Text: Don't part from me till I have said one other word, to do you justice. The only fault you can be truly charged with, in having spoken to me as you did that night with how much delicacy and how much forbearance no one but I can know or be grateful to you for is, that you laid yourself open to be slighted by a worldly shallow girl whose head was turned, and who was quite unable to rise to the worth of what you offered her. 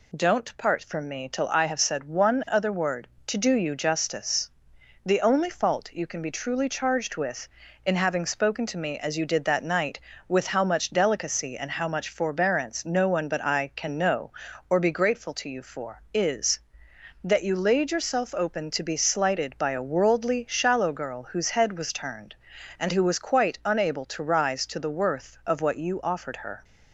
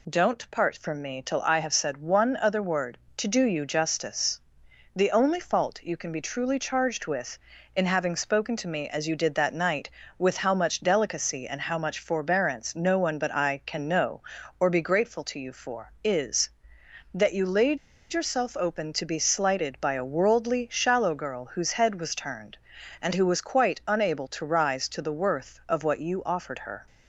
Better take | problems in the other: first | pauses between "laid" and "yourself"; slight; at 17.7 s; 0.34 s long

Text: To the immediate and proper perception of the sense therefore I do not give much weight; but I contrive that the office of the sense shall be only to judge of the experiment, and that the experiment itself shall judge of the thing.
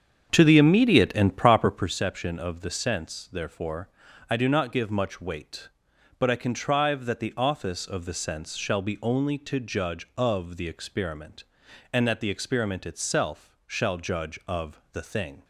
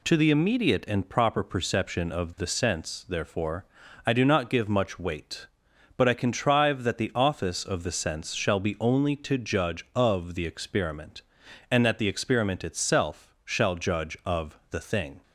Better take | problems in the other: second | starts louder than the rest; strong; until 2.0 s; 7.5 dB // pauses between "therefore" and "I"; at 3.8 s; 0.42 s long; also in the second

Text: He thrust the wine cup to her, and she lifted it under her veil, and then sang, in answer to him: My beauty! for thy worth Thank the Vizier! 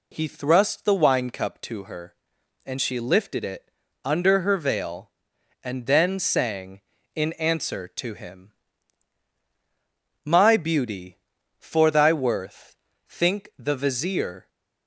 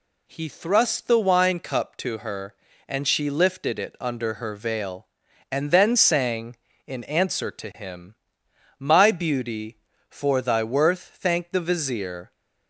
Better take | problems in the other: second | pauses between "it" and "under"; slight; at 3.6 s; 0.34 s long // says "Think" for "Thank"; at 13.0 s

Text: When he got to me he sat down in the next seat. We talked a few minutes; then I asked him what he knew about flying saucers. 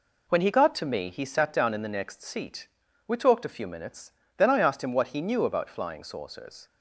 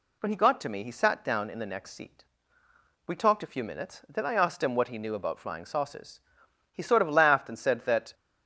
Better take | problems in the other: first | goes on to say "He sort of laughed and said that"; from 6.7 s on; 1.4 s long

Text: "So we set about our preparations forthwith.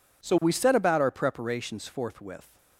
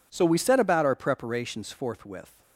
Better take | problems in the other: neither | none

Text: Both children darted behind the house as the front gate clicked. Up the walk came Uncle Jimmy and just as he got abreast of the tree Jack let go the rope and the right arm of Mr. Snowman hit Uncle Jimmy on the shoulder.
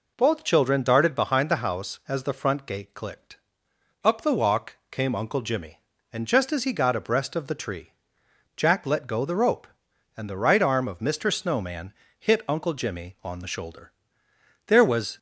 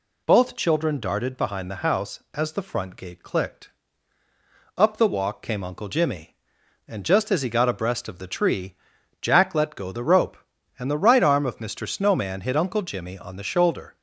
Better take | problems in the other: second | pauses between "walk" and "came"; slight; at 4.7 s; 0.16 s long // pauses between "tree" and "Jack"; noticeable; at 7.9 s; 0.64 s long; noticeable in the second // pauses between "Snowman" and "hit"; slight; at 11.9 s; 0.28 s long // goes on to say "There was"; from 14.6 s on; 0.50 s long

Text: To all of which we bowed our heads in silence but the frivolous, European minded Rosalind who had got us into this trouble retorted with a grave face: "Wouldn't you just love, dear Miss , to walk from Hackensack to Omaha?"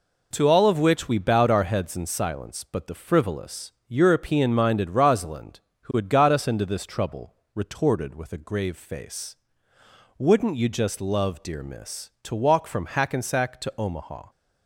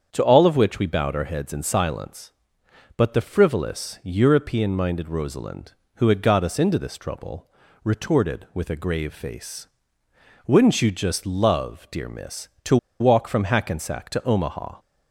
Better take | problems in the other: first | starts louder than the rest; strong; until 1.1 s; 7.5 dB // pauses between "trouble" and "retorted"; slight; at 7.4 s; 0.36 s long; slight in the first // pauses between "to" and "walk"; slight; at 12.7 s; 0.23 s long

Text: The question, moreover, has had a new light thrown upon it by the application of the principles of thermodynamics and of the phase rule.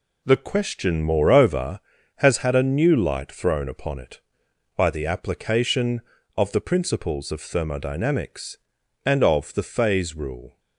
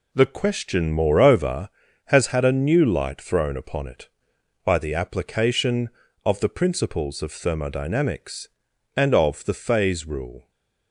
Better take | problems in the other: neither | none

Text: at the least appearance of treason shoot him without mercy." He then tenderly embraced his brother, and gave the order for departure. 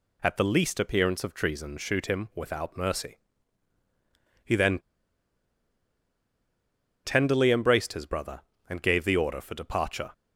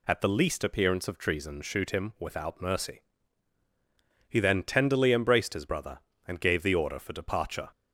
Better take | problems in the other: second | pauses between "then" and "tenderly"; strong; at 4.7 s; 2.2 s long

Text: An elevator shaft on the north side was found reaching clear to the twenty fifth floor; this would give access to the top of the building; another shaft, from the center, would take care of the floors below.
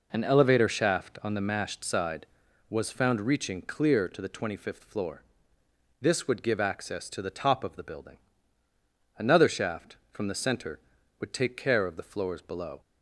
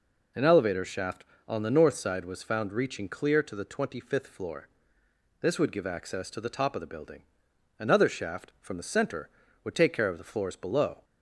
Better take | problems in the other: second | says "mashed" for "north"; at 1.4 s

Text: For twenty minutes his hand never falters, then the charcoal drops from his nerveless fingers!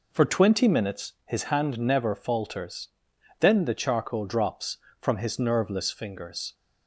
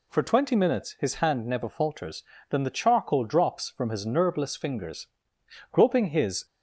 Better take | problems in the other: first | goes on to say "Groping his"; noticeable; from 5.7 s on; 0.74 s long

